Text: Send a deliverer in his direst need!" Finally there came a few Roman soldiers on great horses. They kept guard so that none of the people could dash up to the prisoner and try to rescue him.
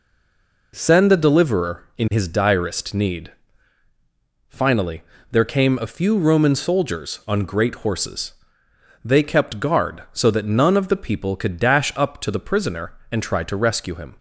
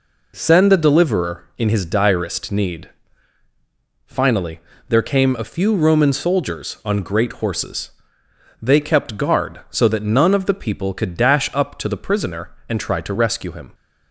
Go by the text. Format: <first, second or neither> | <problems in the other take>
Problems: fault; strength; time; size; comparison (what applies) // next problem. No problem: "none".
second | stays silent before the first word; slight; until 0.7 s; 0.7 s long // pauses between "Finally" and "there"; slight; at 5.0 s; 0.30 s long; slight in the second